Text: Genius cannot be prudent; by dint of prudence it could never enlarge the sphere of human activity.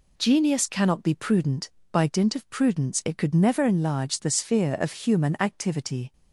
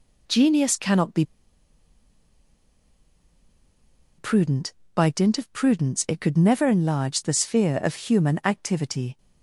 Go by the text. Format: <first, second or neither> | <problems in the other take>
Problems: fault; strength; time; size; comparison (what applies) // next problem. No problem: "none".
first | pauses between "be" and "prudent"; strong; at 1.2 s; 2.9 s long